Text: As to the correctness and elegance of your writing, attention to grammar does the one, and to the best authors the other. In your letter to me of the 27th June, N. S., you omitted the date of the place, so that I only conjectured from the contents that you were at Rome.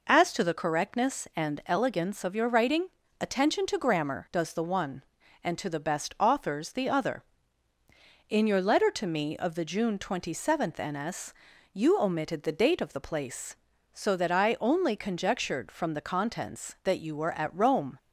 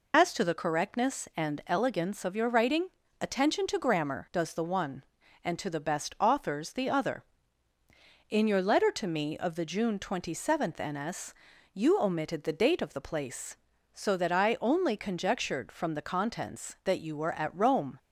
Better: first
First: none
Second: loses the start of "As"; at 0.1 s; 75 ms

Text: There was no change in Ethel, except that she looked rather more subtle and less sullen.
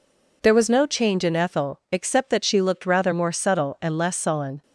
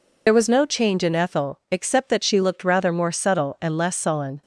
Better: first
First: none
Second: loses the start of "There"; at 0.2 s; 60 ms

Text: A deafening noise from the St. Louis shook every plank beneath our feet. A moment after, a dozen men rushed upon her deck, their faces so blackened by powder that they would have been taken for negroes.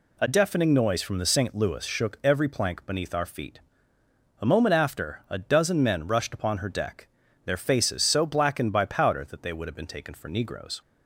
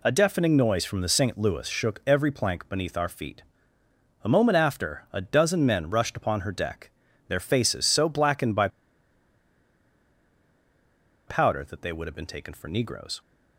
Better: first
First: none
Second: pauses between "by" and "powder"; strong; at 8.6 s; 2.5 s long

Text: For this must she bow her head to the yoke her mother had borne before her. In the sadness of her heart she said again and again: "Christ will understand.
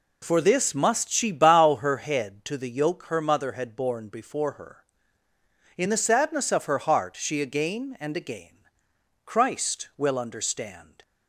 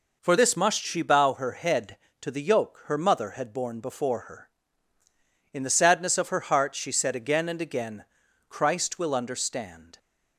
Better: second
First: skips "said"; at 7.4 s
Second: none

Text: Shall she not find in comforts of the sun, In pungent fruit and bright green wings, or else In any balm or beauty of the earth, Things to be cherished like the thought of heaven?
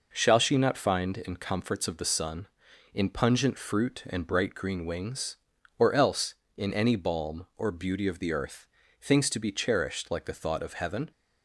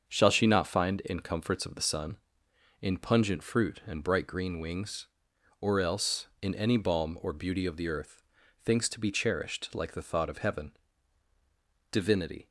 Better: first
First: none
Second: starts louder than the rest; until 1.1 s; 7 dB // goes on to say "Divinity"; from 11.9 s on; 0.58 s long

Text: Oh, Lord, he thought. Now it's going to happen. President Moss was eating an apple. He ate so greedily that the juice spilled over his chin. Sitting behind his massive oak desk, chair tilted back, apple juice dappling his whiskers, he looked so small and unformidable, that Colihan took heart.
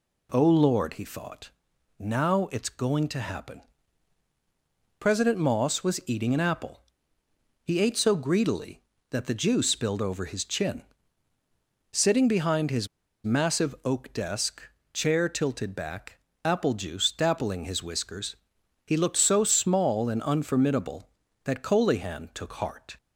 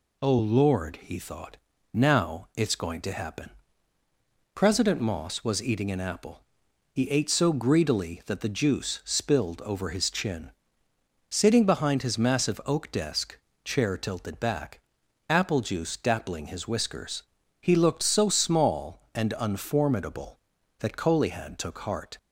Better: second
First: pauses between "his" and "massive"; at 12.8 s; 0.37 s long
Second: none

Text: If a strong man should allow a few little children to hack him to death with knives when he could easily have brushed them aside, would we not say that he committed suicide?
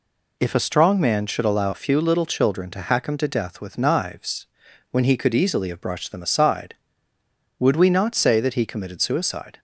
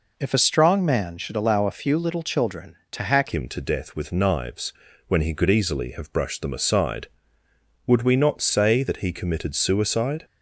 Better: first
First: pauses between "knives" and "when"; at 4.4 s; 0.42 s long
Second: changes voice at "him"; from 3.3 s on; 6.9 s long // pauses between "knives" and "when"; slight; at 4.7 s; 0.34 s long

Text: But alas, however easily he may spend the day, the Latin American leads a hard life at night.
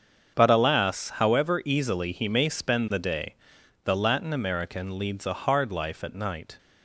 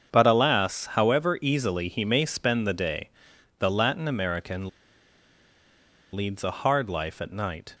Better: first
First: starts louder than the rest; strong; until 1.4 s; 7.5 dB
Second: starts louder than the rest; strong; until 1.2 s; 7.5 dB // pauses between "American" and "leads"; strong; at 4.6 s; 1.4 s long

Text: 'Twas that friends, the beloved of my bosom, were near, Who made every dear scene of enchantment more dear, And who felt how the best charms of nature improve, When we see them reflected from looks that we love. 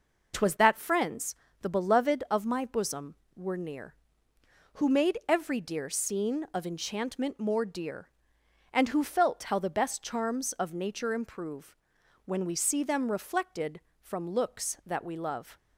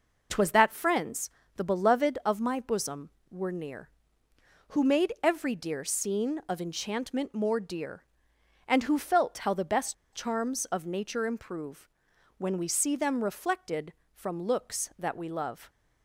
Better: first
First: none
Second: pauses between "best" and "charms"; slight; at 9.9 s; 0.20 s long

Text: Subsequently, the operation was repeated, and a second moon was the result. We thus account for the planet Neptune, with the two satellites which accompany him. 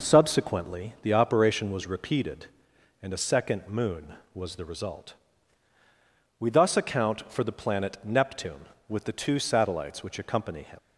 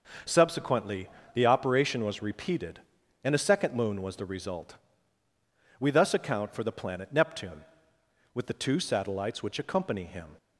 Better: second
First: leaves "him" unfinished; at 10.7 s; 65 ms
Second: none

